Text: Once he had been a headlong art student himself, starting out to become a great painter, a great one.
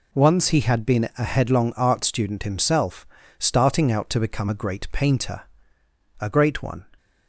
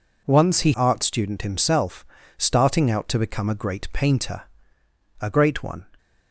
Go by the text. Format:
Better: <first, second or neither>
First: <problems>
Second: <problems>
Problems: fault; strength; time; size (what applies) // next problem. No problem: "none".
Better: first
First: none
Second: skips "had been a headlong"; at 0.7 s